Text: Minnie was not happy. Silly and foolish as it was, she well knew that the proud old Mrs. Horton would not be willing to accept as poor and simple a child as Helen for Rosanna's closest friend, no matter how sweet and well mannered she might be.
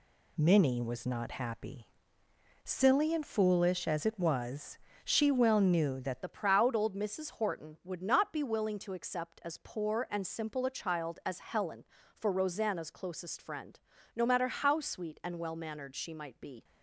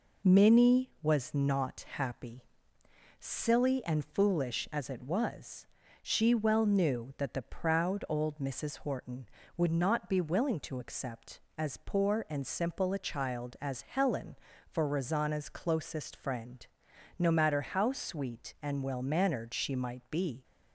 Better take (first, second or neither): second